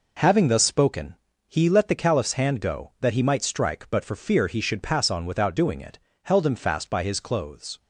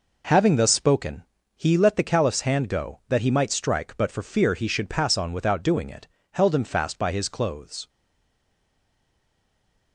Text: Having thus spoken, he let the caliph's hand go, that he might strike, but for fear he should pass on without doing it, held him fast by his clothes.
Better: first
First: none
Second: stays silent after the last word; noticeable; from 7.8 s on; 2.1 s long

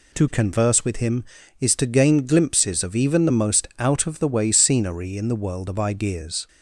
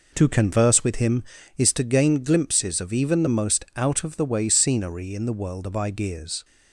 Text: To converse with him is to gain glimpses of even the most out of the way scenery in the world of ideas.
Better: first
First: none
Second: starts louder than the rest; noticeable; until 1.8 s; 5 dB

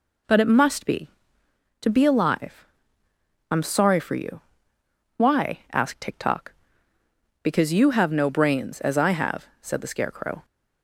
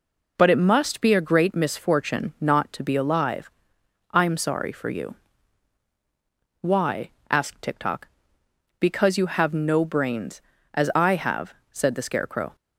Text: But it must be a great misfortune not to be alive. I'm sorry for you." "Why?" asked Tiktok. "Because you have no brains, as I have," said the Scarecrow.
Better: second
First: skips "a great misfortune not"; at 1.4 s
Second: none

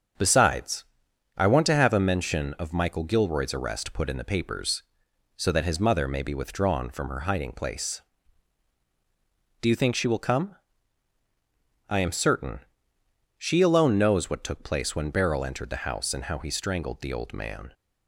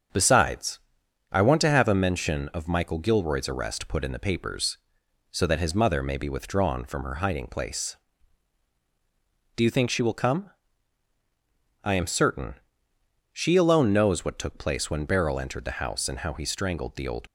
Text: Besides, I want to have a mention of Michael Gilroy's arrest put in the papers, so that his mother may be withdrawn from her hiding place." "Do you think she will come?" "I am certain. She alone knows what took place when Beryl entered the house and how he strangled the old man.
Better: first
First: starts louder than the rest; strong; until 1.7 s; 7 dB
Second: starts louder than the rest; strong; until 1.6 s; 7 dB // stops before "man"; at 17.2 s

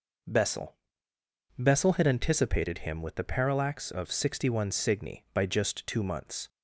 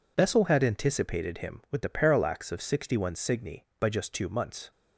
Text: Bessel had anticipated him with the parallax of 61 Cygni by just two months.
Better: second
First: says "Bessel" twice; at 1.5 s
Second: none

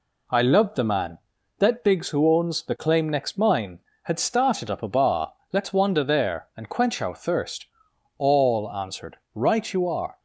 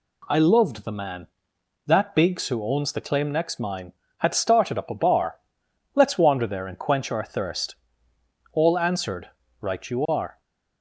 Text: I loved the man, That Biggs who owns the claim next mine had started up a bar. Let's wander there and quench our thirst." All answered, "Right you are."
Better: neither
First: none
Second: none

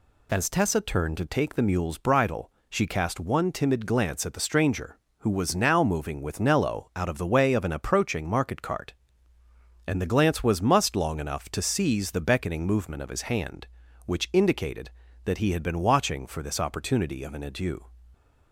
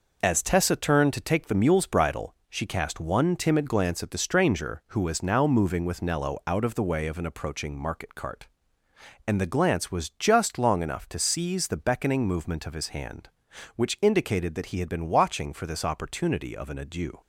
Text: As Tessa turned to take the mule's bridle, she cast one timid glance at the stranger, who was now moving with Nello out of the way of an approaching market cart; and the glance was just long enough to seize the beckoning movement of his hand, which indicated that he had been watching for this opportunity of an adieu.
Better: second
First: says "must" for "just"; at 10.6 s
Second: none

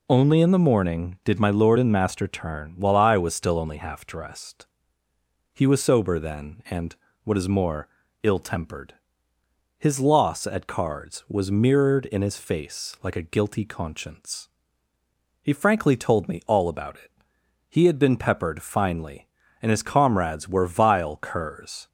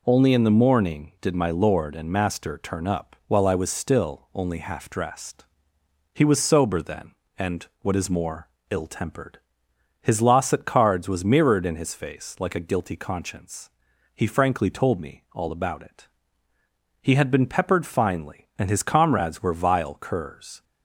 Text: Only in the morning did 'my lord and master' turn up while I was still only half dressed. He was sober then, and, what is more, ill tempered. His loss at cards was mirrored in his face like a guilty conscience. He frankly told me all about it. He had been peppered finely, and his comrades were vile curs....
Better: second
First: skips "up"; at 2.7 s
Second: none

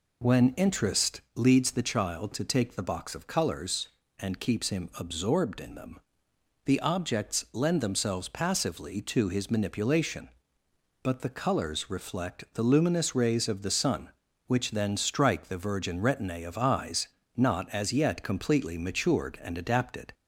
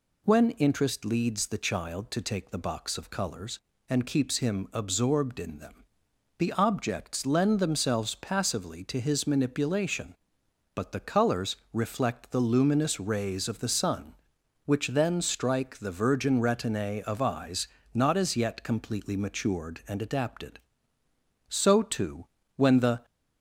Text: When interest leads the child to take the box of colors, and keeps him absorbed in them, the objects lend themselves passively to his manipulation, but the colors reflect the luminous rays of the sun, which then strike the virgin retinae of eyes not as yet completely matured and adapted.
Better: first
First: pauses between "eyes" and "not"; slight; at 17.0 s; 0.28 s long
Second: pauses between "colors" and "reflect"; slight; at 11.5 s; 0.16 s long // pauses between "eyes" and "not"; slight; at 17.6 s; 0.26 s long // goes on to say "So too when the"; from 21.5 s on; 1.5 s long

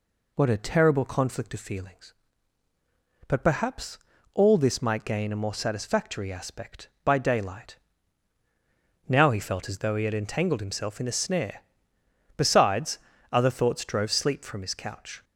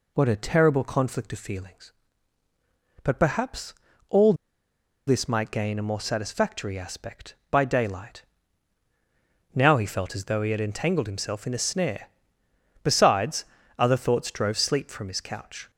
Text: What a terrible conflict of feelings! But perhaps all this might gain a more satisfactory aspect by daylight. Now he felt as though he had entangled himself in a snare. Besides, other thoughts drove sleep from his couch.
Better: first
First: pauses between "perhaps" and "all"; slight; at 3.9 s; 0.36 s long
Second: pauses between "perhaps" and "all"; slight; at 3.7 s; 0.36 s long // pauses between "all" and "this"; noticeable; at 4.3 s; 0.73 s long

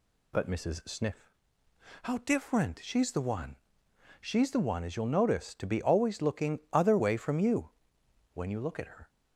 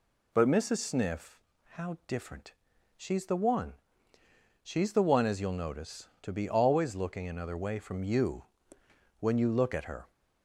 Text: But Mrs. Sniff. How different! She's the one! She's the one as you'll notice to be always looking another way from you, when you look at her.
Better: second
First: says "other" for "another"; at 6.7 s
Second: none

